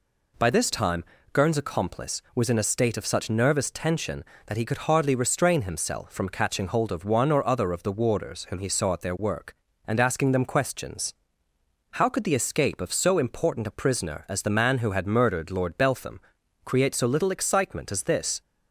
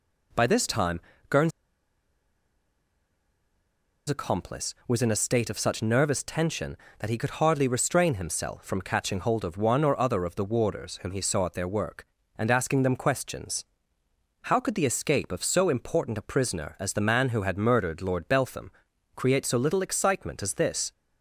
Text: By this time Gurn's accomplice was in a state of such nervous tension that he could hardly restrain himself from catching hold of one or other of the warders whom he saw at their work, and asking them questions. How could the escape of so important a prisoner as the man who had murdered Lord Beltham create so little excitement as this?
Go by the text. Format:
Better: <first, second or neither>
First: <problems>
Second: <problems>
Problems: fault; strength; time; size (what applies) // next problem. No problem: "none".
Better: first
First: pauses between "time" and "Gurn's"; slight; at 1.0 s; 0.30 s long // pauses between "Beltham" and "create"; noticeable; at 16.1 s; 0.46 s long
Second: pauses between "time" and "Gurn's"; slight; at 0.9 s; 0.30 s long // pauses between "Gurn's" and "accomplice"; strong; at 1.5 s; 2.5 s long // pauses between "Beltham" and "create"; noticeable; at 18.6 s; 0.46 s long